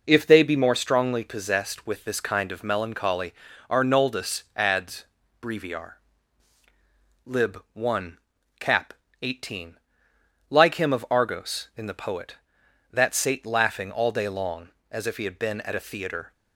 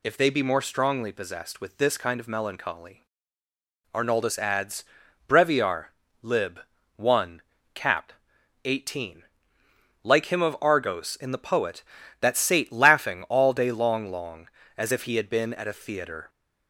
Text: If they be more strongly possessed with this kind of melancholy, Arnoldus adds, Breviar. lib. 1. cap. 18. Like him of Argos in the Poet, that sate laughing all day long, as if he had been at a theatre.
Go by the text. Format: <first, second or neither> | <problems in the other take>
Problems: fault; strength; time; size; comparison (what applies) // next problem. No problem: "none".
first | says "long" twice; at 14.1 s